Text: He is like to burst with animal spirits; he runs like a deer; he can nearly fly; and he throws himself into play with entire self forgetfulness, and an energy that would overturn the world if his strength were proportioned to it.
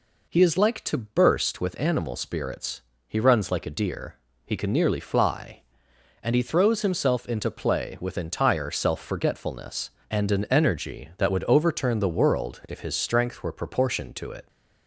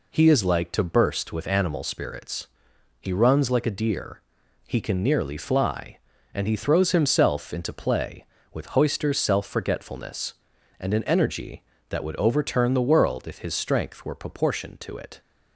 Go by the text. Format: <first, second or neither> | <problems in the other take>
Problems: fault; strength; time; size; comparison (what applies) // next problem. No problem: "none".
first | says "hoister" for "entire"; at 8.7 s